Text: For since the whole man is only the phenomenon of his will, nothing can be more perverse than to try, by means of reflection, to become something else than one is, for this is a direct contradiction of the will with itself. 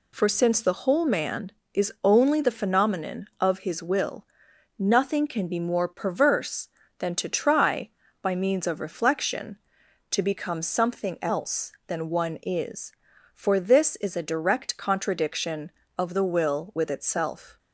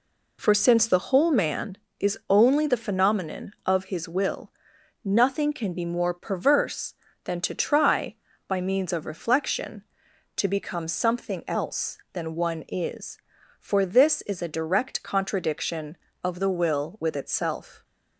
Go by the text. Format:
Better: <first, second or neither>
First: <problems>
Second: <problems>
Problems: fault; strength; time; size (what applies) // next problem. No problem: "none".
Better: first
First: none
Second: starts louder than the rest; slight; until 1.7 s; 3 dB